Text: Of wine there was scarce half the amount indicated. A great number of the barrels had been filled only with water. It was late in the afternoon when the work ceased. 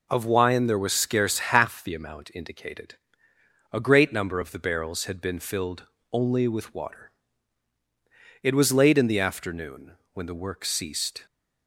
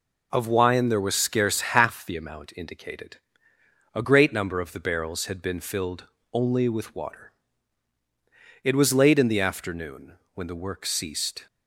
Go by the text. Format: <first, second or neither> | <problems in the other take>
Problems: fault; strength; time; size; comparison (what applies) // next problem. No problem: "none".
neither | pauses between "filled" and "only"; slight; the same in both // pauses between "afternoon" and "when"; slight; the same in both